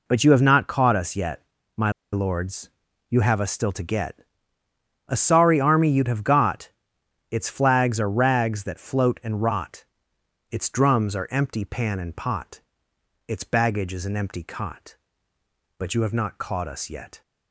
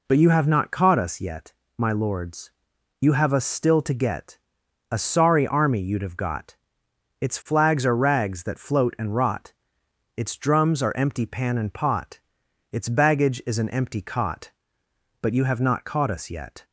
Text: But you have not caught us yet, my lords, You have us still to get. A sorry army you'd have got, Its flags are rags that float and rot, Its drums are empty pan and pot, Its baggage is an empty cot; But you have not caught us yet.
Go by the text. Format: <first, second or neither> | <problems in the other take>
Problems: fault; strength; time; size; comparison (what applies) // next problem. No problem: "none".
second | pauses between "my" and "lords"; slight; at 1.9 s; 0.21 s long